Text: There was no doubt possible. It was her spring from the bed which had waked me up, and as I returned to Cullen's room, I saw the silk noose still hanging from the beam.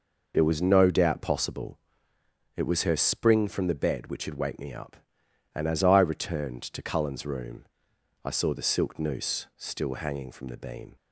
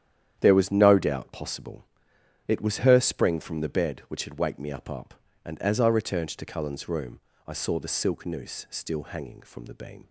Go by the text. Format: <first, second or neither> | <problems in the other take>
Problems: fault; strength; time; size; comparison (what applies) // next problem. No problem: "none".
first | starts louder than the rest; strong; until 1.4 s; 9.5 dB // says "up" twice; at 4.9 s